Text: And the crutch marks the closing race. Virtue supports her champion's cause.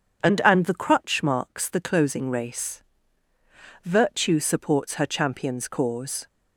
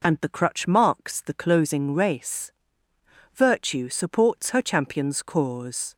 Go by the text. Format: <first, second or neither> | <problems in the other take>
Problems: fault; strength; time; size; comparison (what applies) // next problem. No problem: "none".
second | starts louder than the rest; strong; until 1.2 s; 7.5 dB // says "And" twice; at 0.4 s